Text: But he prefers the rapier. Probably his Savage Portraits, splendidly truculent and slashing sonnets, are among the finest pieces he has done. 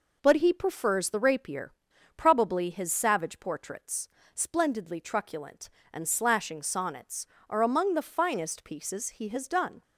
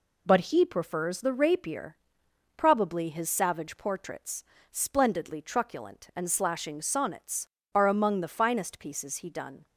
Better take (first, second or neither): first